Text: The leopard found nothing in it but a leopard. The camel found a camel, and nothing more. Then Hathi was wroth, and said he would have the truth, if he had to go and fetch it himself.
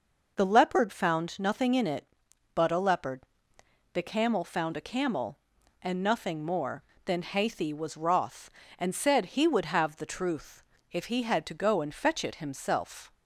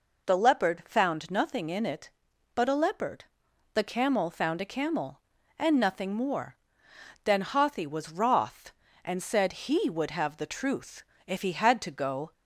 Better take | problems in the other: first | stops before "and fetch it himself"; at 12.3 s

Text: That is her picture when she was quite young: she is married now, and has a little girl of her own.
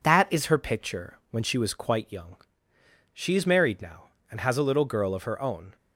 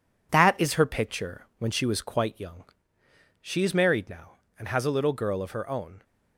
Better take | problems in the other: first | gets quieter; noticeable; throughout; 5 dB

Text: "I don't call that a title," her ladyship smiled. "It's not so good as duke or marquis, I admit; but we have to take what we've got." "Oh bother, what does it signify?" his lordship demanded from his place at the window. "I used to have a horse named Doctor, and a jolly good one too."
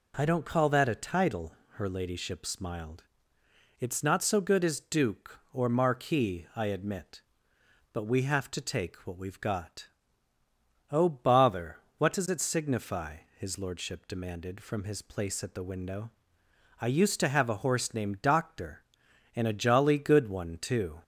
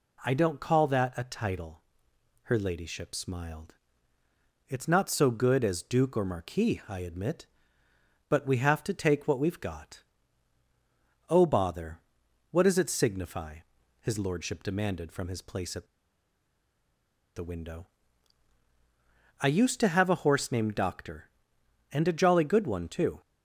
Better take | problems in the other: first | pauses between "at" and "the"; strong; at 15.8 s; 1.5 s long

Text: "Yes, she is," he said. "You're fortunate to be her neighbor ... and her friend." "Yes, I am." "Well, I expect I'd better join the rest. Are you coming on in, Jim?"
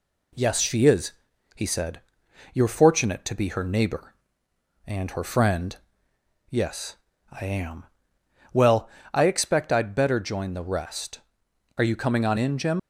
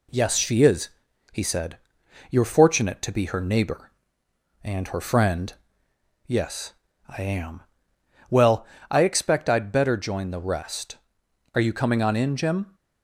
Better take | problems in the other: second | leaves "Jim" unfinished; at 12.7 s; 170 ms

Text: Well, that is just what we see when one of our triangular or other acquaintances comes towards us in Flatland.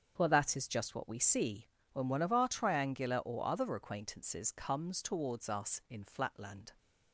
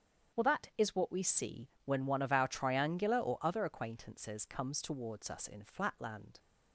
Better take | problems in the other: first | starts louder than the rest; strong; until 1.4 s; 8.5 dB; also in the first // skips "just"; at 0.9 s // pauses between "see" and "when"; slight; at 1.6 s; 0.16 s long; slight in the first

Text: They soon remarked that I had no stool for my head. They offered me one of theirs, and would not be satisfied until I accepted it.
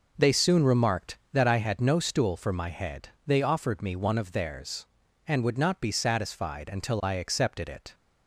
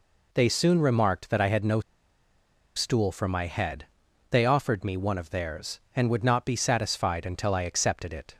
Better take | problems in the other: first | pauses between "no" and "stool"; noticeable; at 1.8 s; 0.95 s long

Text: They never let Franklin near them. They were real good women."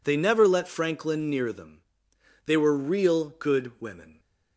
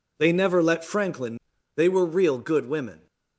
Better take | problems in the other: first | skips "near them"; at 1.5 s

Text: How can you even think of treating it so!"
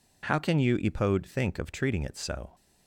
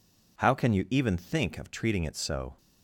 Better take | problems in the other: second | says "epode" for "even"; at 0.7 s

